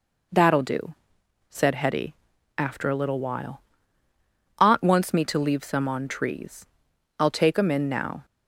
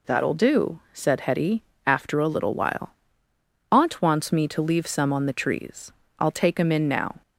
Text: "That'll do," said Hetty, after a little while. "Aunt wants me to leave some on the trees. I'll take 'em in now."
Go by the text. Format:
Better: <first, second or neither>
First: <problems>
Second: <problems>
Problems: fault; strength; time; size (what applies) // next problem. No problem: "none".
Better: second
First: skips "the"; at 6.0 s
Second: none